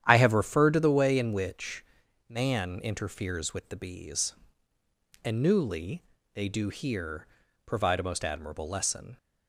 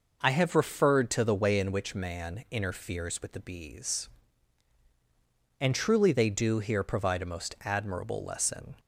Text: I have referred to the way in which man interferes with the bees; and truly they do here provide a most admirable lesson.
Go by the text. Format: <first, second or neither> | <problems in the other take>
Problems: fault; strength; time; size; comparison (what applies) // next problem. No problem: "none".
second | starts louder than the rest; strong; until 1.0 s; 10 dB // pauses between "which" and "man"; at 1.8 s; 0.42 s long // says "newly" for "truly"; at 5.4 s // pauses between "here" and "provide"; at 7.2 s; 0.40 s long